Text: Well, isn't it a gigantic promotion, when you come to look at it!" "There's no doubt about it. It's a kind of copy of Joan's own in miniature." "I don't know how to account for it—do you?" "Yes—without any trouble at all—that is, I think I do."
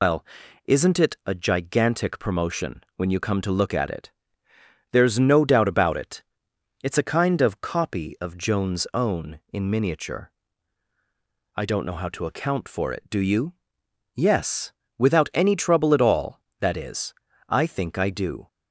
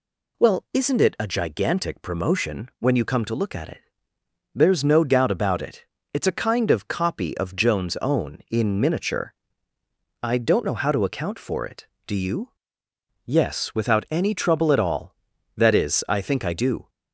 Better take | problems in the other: second | loses the start of "Well"; at 0.0 s; 110 ms

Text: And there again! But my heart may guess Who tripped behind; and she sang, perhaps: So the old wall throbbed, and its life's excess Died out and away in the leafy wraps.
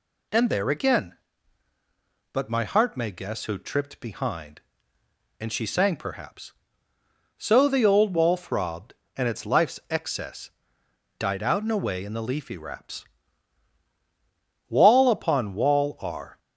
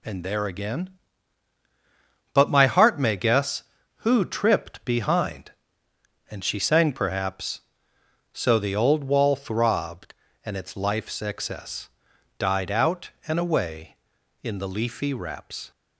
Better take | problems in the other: second | pauses between "excess" and "Died"; noticeable; at 10.5 s; 0.68 s long; noticeable in the second // goes on to say "Wall upon wall are"; strong; from 14.6 s on; 1.7 s long

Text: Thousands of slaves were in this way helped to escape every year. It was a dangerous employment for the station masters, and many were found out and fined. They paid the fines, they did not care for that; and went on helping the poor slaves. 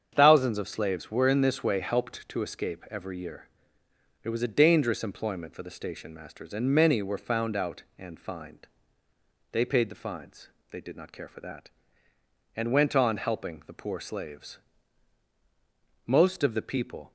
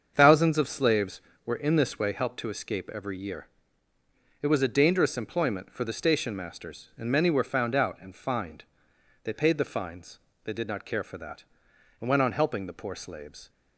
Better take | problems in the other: second | starts louder than the rest; strong; until 1.1 s; 7.5 dB; also in the second // goes on to say "Most of the people"; noticeable; from 16.0 s on; 1.0 s long

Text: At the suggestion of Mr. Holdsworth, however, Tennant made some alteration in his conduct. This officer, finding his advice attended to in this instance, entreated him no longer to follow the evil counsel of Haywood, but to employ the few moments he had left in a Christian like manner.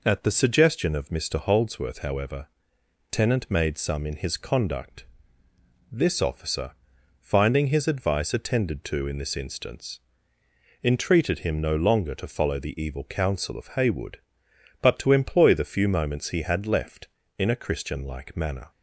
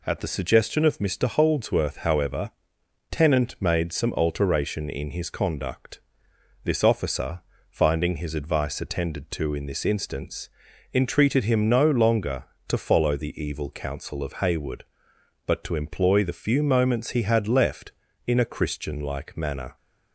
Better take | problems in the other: second | skips "alteration"; at 4.0 s

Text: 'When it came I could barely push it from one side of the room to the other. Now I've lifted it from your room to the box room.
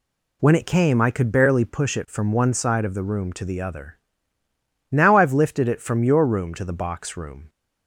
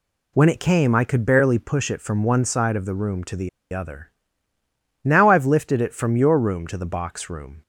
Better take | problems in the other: first | pauses between "the" and "other"; slight; at 3.4 s; 0.24 s long

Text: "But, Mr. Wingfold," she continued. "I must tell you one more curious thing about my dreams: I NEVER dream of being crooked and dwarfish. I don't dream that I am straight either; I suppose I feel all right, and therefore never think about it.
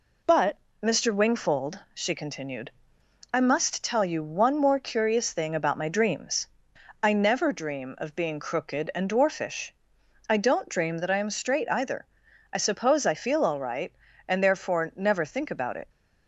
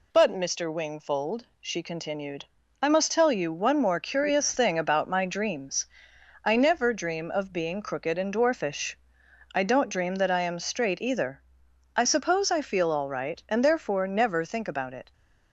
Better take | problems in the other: neither | none

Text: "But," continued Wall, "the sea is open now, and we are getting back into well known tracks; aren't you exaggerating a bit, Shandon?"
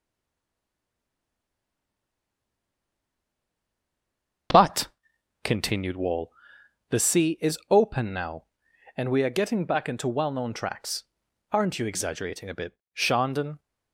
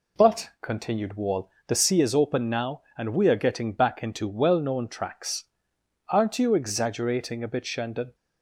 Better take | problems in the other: second | stays silent before the first word; strong; until 4.5 s; 4.5 s long // starts louder than the rest; until 6.0 s; 7 dB

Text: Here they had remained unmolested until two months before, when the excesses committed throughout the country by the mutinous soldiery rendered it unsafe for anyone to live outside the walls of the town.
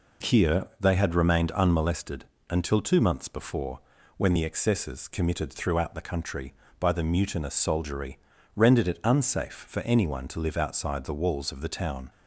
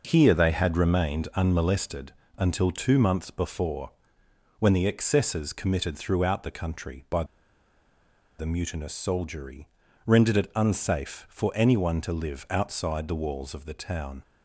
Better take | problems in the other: first | pauses between "unmolested" and "until"; slight; at 2.1 s; 0.26 s long; slight in the first // pauses between "by" and "the"; at 7.2 s; 1.1 s long // pauses between "soldiery" and "rendered"; at 9.6 s; 0.38 s long; slight in the first

